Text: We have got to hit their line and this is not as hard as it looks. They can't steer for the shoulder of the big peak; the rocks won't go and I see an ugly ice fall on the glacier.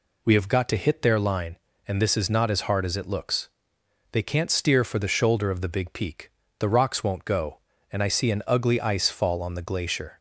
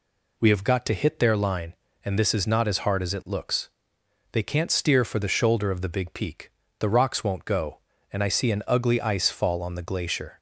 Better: neither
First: none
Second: none

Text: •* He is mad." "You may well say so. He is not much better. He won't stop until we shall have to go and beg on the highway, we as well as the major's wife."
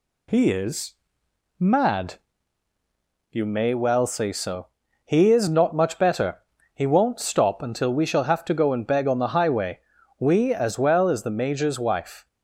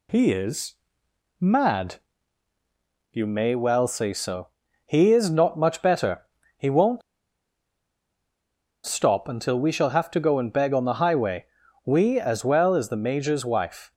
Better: first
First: pauses between "is" and "mad"; noticeable; at 0.9 s; 0.64 s long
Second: pauses between "is" and "mad"; noticeable; at 0.7 s; 0.64 s long // pauses between "won't" and "stop"; strong; at 7.0 s; 1.8 s long

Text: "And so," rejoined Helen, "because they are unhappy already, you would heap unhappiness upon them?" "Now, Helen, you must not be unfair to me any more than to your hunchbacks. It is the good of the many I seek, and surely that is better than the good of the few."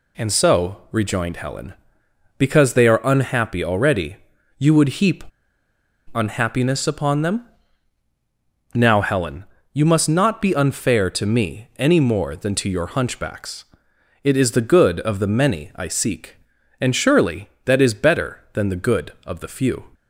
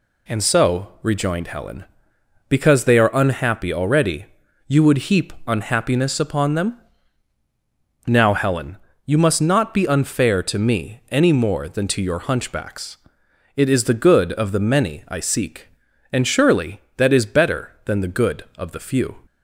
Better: second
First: pauses between "heap" and "unhappiness"; noticeable; at 5.2 s; 0.90 s long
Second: none

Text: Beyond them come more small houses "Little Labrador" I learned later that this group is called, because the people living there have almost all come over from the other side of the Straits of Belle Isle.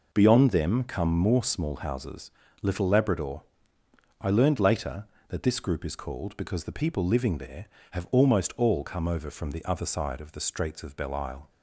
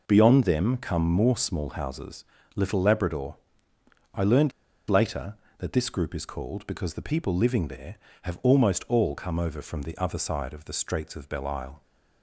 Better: first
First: pauses between "houses" and "Little"; slight; at 2.3 s; 0.30 s long // pauses between "Labrador" and "I"; noticeable; at 3.4 s; 0.76 s long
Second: pauses between "houses" and "Little"; slight; at 2.2 s; 0.30 s long // pauses between "Labrador" and "I"; noticeable; at 3.3 s; 0.76 s long // pauses between "learned" and "later"; at 4.5 s; 0.37 s long

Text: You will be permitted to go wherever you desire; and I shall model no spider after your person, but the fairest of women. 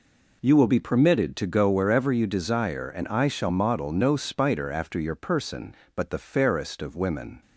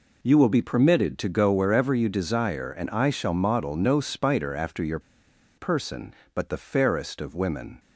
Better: first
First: none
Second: pauses between "your" and "person"; noticeable; at 4.9 s; 0.58 s long

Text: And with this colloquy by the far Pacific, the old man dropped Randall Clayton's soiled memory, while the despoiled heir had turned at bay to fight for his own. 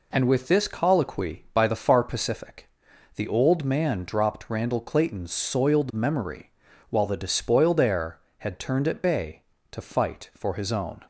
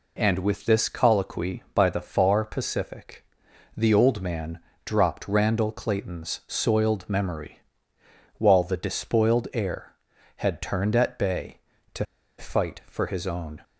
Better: first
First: none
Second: pauses between "man" and "dropped"; slight; at 4.5 s; 0.26 s long // pauses between "to" and "fight"; slight; at 12.0 s; 0.35 s long

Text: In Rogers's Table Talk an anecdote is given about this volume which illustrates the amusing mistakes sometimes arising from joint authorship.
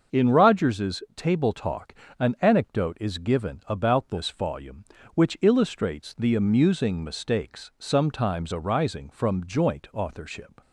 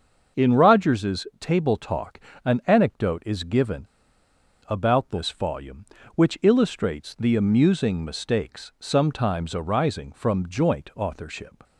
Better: first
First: starts louder than the rest; until 1.2 s; 6.5 dB // pauses between "Talk" and "an"; slight; at 1.9 s; 0.26 s long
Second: starts louder than the rest; until 1.4 s; 6.5 dB // pauses between "Talk" and "an"; slight; at 2.1 s; 0.26 s long // pauses between "given" and "about"; noticeable; at 3.8 s; 0.81 s long

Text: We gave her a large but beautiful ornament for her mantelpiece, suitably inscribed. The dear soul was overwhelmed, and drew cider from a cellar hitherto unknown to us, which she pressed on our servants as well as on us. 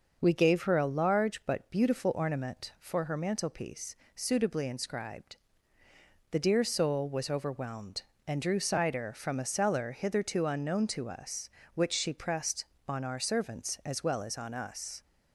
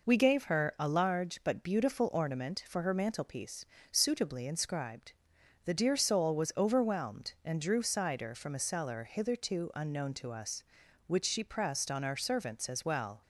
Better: first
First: none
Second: stops before "as on us"; at 13.2 s

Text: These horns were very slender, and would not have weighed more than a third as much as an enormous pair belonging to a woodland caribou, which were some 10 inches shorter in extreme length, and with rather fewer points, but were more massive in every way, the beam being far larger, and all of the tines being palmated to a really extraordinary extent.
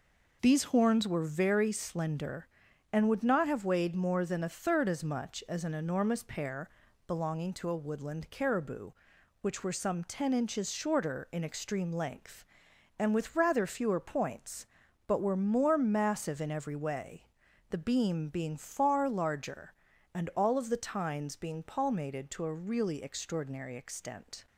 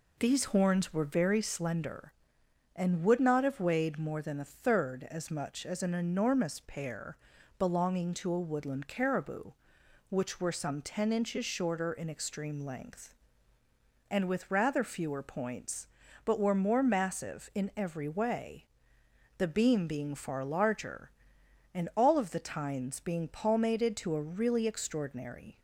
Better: first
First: pauses between "pair" and "belonging"; slight; at 6.7 s; 0.36 s long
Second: pauses between "pair" and "belonging"; at 7.1 s; 0.42 s long // stops before "extent"; at 25.5 s

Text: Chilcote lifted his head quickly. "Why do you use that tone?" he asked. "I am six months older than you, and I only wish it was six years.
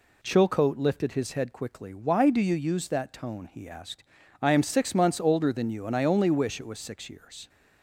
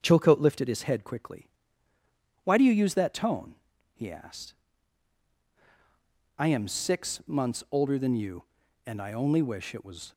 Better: first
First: none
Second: starts louder than the rest; strong; until 1.0 s; 7 dB // stops before "six years"; at 10.1 s

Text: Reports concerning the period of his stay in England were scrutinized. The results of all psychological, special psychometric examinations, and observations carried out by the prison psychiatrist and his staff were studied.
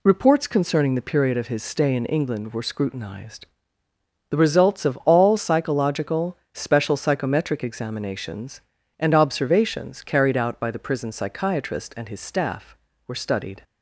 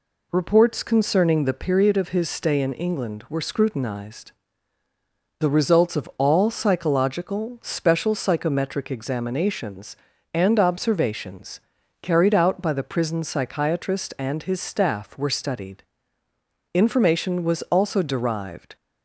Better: first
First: none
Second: pauses between "observations" and "carried"; at 11.5 s; 0.44 s long // goes on to say "Information was also derived"; strong; from 16.7 s on; 2.0 s long

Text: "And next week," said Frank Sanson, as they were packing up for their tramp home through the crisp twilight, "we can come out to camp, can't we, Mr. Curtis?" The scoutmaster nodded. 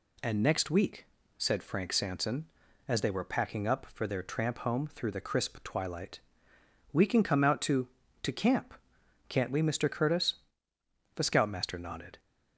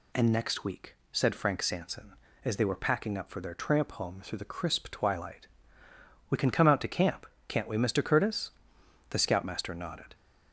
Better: second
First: says "to" twice; at 8.2 s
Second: none

